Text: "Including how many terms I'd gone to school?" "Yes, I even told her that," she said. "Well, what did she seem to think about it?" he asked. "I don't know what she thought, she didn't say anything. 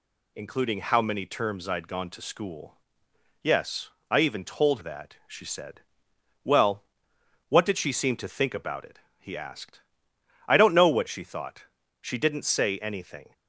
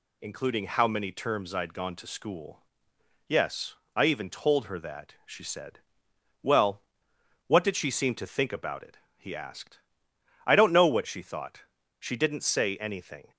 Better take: second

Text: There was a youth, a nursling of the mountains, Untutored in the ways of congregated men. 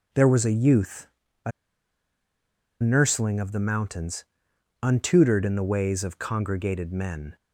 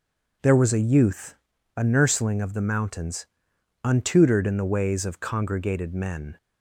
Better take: second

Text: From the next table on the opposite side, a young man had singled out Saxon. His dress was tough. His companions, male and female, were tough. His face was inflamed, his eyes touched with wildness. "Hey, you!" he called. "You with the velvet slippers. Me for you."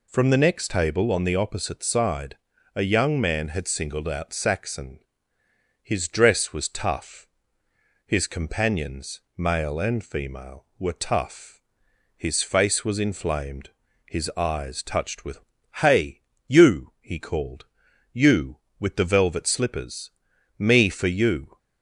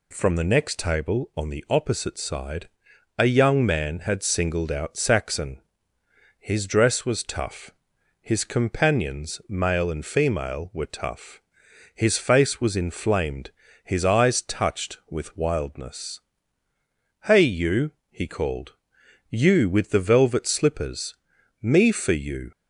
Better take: second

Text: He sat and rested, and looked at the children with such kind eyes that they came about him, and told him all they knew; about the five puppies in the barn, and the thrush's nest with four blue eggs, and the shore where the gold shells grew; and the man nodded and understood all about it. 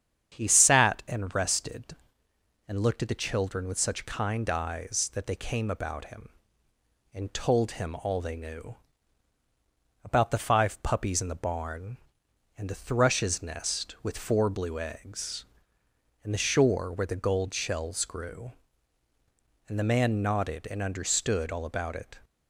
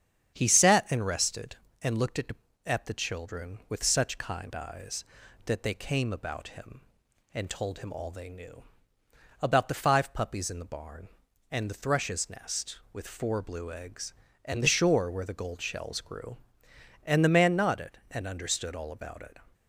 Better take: first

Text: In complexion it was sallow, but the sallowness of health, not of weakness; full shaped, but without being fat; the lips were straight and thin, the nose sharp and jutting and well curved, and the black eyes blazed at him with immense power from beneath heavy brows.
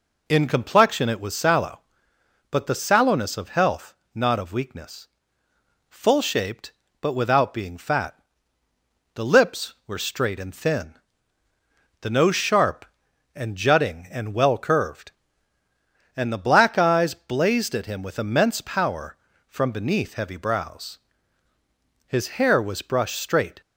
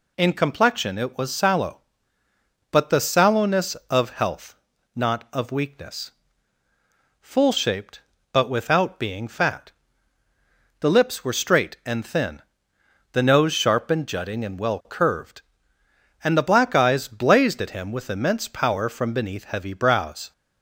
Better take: second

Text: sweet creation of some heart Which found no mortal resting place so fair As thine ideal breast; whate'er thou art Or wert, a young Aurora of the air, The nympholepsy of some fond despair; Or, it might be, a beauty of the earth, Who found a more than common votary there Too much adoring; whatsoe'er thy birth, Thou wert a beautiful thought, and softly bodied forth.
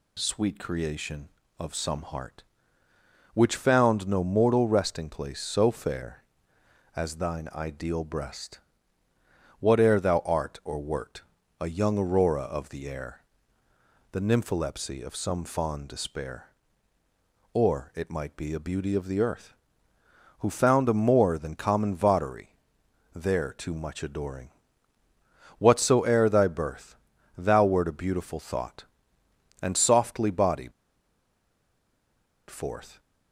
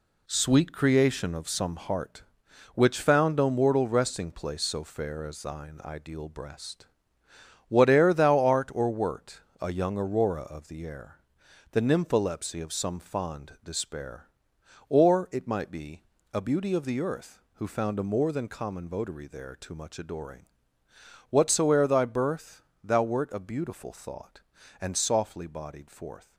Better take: second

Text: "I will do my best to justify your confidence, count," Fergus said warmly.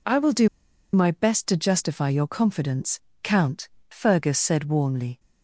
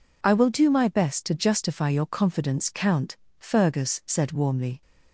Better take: second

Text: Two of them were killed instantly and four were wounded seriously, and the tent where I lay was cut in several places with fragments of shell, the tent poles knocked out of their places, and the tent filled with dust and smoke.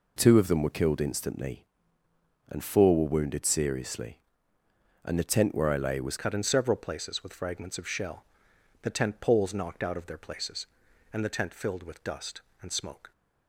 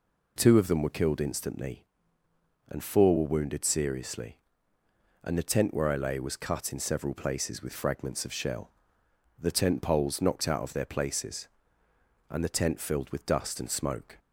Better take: second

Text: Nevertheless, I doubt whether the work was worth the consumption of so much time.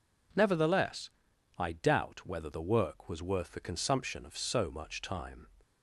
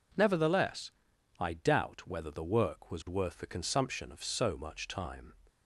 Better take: neither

